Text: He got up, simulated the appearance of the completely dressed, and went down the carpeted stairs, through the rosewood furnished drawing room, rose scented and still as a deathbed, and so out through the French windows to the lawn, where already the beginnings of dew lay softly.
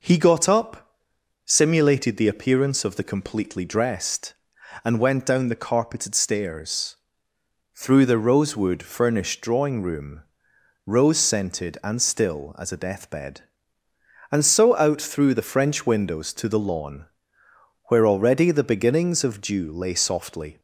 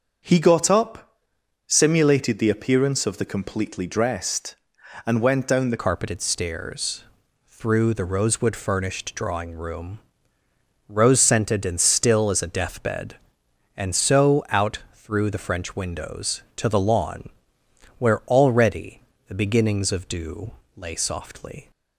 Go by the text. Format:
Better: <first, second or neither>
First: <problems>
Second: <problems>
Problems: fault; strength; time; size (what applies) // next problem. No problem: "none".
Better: first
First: none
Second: changes voice at "carpeted"; from 5.8 s on; 15.9 s long // pauses between "already" and "the"; slight; at 19.0 s; 0.28 s long // pauses between "dew" and "lay"; slight; at 20.5 s; 0.26 s long